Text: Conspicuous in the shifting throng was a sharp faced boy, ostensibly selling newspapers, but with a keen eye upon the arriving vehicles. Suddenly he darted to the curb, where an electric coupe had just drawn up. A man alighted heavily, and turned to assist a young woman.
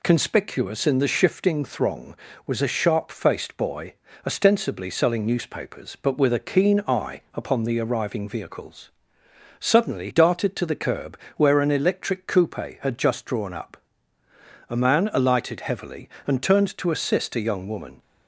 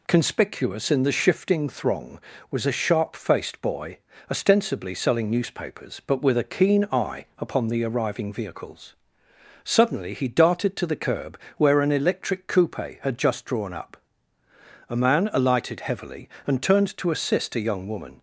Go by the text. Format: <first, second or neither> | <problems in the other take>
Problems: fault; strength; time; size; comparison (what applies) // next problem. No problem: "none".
second | skips "he"; at 10.0 s